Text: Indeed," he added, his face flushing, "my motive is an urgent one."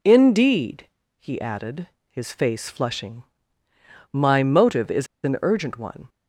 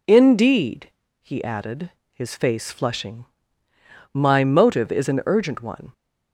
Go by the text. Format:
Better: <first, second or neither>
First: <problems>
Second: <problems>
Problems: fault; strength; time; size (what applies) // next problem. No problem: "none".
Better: second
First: pauses between "is" and "an"; slight; at 5.0 s; 0.18 s long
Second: none